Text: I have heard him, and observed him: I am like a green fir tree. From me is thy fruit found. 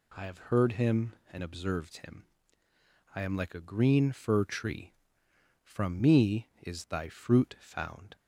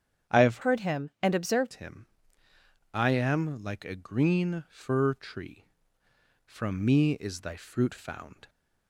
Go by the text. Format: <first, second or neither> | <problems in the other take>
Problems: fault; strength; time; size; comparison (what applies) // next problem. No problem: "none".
first | starts louder than the rest; strong; until 1.4 s; 8.5 dB // changes voice from "heard" to "observed"; from 0.6 to 1.7 s; 1.1 s long